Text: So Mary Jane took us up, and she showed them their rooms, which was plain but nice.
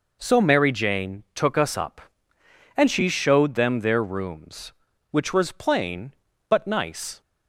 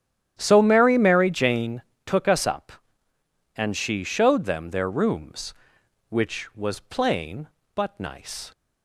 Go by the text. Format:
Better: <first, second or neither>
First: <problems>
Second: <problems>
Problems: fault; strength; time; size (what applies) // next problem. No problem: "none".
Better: first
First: none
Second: starts louder than the rest; strong; until 1.4 s; 10.5 dB // says "Mary" twice; at 0.9 s // pauses between "Jane" and "took"; slight; at 1.8 s; 0.24 s long